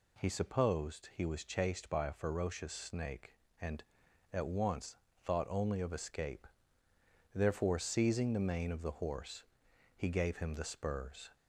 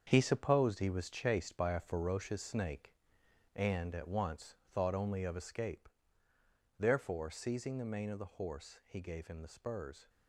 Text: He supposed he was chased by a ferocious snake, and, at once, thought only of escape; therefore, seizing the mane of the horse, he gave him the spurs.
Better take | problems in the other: first | gets quieter; strong; throughout; 9.5 dB

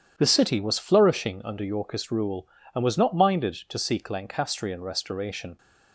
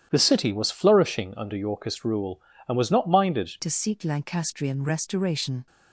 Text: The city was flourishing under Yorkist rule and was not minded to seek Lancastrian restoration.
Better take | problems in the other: first | starts louder than the rest; strong; until 1.1 s; 10 dB // changes voice at "to"; from 3.6 s on; 2.0 s long

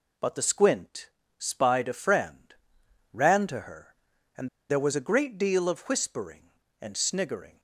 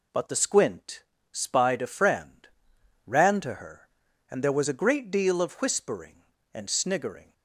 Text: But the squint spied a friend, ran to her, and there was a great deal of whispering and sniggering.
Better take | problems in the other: second | pauses between "squint" and "spied"; slight; at 1.0 s; 0.28 s long; slight in the second // pauses between "and" and "there"; slight; at 4.4 s; 0.21 s long

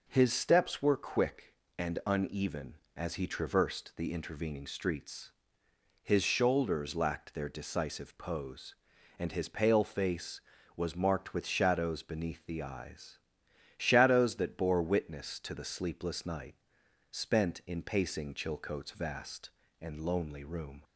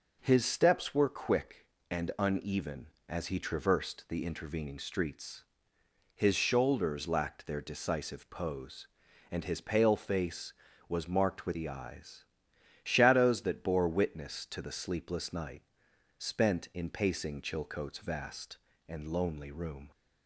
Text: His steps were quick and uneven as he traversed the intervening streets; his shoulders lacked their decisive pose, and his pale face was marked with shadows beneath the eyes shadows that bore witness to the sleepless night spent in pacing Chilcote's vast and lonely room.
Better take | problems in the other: first | skips "shadows beneath"; at 11.5 s // pauses between "eyes" and "shadows"; noticeable; at 12.2 s; 0.60 s long; noticeable in the first // pauses between "night" and "spent"; noticeable; at 15.6 s; 0.56 s long; noticeable in the first

